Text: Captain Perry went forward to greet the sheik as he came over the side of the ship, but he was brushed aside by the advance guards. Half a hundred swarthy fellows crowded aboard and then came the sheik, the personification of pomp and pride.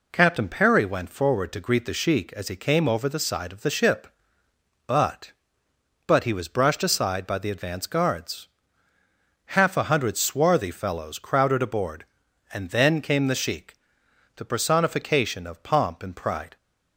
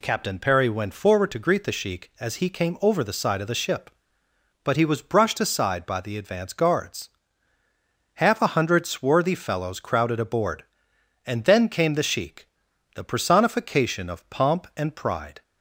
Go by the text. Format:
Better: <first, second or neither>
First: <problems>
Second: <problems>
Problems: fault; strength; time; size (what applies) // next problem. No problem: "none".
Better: second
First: says "but" twice; at 6.0 s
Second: none